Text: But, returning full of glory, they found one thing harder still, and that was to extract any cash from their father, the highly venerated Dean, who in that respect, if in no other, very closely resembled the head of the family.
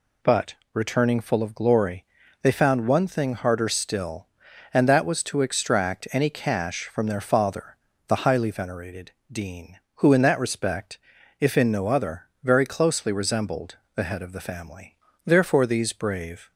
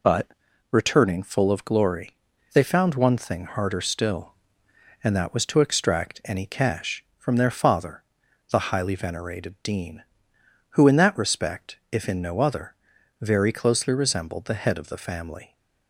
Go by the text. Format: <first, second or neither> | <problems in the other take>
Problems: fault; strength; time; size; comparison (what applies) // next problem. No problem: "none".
second | pauses between "venerated" and "Dean"; slight; at 9.1 s; 0.20 s long // pauses between "resembled" and "the"; slight; at 13.7 s; 0.18 s long // goes on to say "Therefore these brave"; noticeable; from 15.2 s on; 1.2 s long